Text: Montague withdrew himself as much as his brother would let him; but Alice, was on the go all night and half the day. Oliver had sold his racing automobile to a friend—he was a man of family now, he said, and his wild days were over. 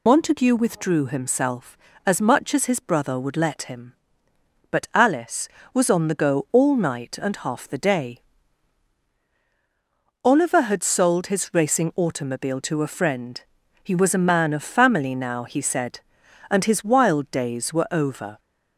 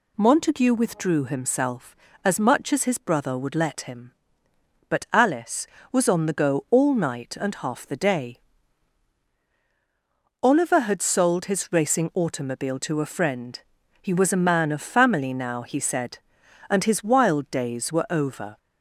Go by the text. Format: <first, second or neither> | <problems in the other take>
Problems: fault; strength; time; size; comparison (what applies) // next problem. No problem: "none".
second | loses the start of "Montague"; at 0.0 s; 80 ms